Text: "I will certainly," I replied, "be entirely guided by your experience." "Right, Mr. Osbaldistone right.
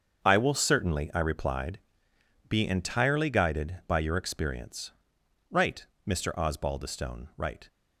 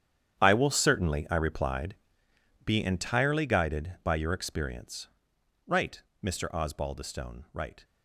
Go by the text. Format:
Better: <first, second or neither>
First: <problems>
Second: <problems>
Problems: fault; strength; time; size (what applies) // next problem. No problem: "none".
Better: first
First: starts louder than the rest; until 1.3 s; 7 dB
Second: gets quieter; strong; throughout; 15 dB // starts louder than the rest; strong; until 1.4 s; 9.5 dB